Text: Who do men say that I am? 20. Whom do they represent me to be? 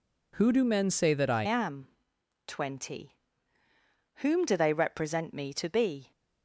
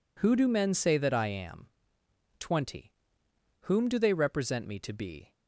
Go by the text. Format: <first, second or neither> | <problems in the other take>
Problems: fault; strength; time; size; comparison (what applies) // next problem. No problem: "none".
second | changes voice at "am"; from 1.4 s on; 4.7 s long